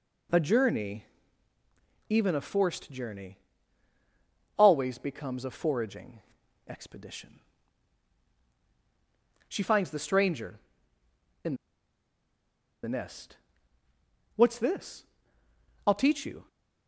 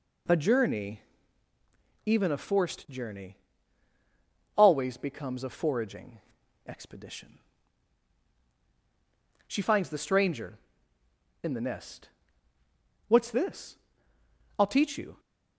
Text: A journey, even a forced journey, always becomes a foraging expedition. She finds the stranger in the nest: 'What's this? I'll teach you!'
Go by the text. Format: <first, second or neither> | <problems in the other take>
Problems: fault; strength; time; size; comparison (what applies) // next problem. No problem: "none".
second | pauses between "foraging" and "expedition"; noticeable; at 6.2 s; 0.48 s long; noticeable in the second // pauses between "in" and "the"; strong; at 11.5 s; 1.2 s long